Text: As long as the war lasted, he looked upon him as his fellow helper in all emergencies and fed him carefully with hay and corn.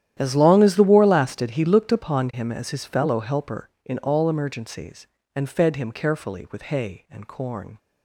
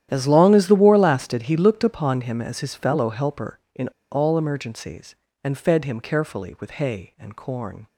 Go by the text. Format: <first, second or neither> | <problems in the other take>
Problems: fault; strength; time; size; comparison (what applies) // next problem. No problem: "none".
first | starts louder than the rest; strong; until 1.1 s; 11 dB; strong in the first // pauses between "in" and "all"; slight; at 3.8 s; 0.23 s long